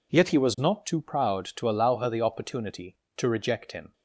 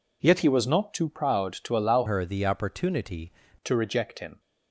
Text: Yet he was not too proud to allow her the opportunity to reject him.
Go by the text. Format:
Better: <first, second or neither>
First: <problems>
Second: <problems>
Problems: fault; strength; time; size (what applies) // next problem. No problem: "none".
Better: first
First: none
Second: changes voice from "her" to "opportunity"; from 2.0 to 3.3 s; 1.3 s long